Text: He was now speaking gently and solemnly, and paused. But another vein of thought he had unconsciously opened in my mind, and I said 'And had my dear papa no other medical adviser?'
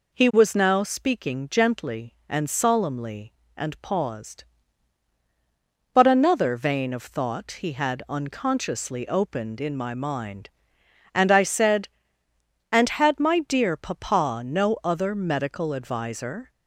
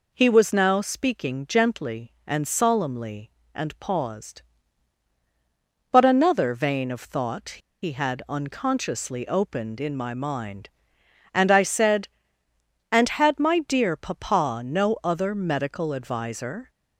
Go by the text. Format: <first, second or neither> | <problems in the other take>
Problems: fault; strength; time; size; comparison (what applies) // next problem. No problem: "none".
first | pauses between "thought" and "he"; slight; at 7.5 s; 0.26 s long